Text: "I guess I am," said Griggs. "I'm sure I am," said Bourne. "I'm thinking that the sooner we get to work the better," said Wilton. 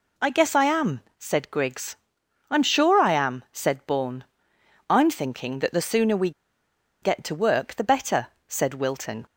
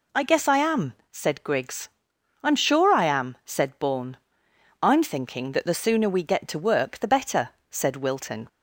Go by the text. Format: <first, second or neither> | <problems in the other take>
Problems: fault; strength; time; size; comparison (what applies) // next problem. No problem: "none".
second | pauses between "we" and "get"; noticeable; at 6.3 s; 0.72 s long